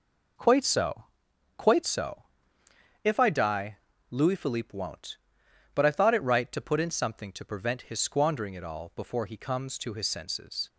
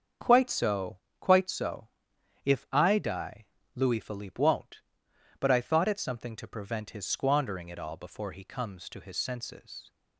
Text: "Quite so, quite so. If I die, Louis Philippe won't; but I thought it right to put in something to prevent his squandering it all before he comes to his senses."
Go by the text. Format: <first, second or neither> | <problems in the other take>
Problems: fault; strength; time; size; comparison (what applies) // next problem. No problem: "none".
first | starts louder than the rest; until 1.4 s; 7 dB // skips "right to put in"; at 5.9 s